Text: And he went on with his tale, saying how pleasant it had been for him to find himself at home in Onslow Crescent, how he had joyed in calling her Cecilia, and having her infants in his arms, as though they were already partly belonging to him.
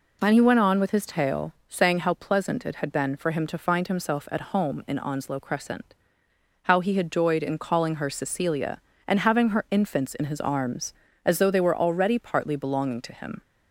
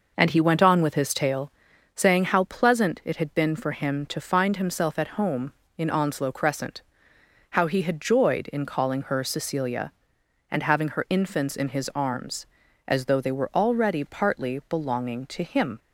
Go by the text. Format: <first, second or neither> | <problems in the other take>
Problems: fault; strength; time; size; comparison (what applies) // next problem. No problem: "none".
first | starts louder than the rest; noticeable; until 1.9 s; 5.5 dB